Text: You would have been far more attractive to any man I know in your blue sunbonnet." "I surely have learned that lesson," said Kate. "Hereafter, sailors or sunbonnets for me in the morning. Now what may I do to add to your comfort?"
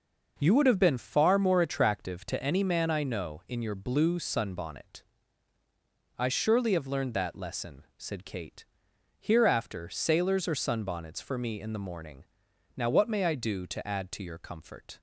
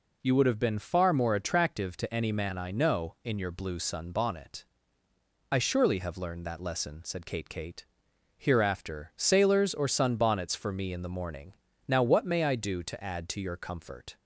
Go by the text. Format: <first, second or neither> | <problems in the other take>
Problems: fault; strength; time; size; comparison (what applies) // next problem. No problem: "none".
first | says "Kate" twice; at 7.4 s